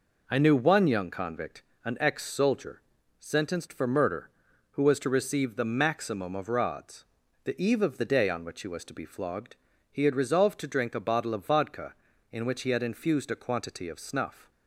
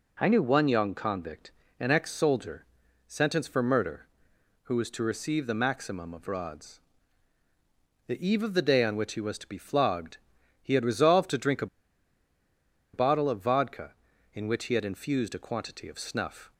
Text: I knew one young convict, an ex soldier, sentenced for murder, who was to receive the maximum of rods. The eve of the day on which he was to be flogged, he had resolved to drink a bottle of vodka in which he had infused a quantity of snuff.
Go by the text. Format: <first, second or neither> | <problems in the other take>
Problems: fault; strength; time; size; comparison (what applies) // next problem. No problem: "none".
first | pauses between "a" and "bottle"; strong; at 11.6 s; 1.2 s long